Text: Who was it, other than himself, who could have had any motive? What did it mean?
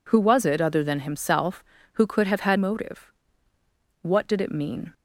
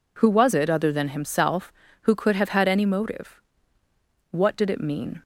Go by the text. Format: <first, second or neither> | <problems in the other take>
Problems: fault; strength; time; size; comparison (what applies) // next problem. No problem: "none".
second | skips "any"; at 2.5 s